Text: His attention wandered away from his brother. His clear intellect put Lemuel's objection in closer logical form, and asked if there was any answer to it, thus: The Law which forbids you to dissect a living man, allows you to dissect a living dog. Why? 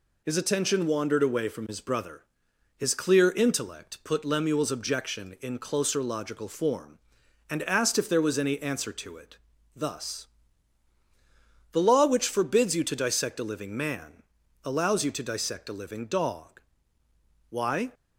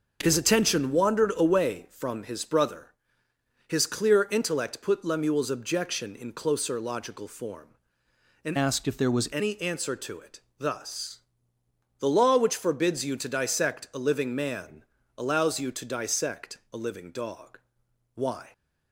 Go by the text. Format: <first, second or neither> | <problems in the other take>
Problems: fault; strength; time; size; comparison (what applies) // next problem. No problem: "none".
first | changes voice from "asked" to "was"; from 8.5 to 9.2 s; 0.7 s long